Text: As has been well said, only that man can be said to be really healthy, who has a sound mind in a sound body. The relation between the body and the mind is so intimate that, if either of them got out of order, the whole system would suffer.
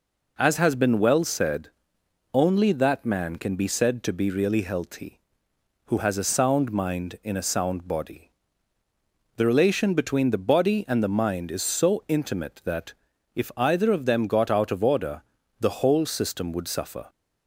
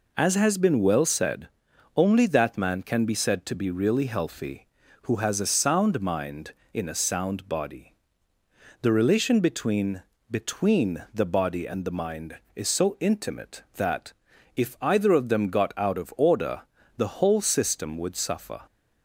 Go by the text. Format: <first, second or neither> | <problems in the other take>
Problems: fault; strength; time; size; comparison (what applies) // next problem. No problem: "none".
first | says "between" twice; at 10.2 s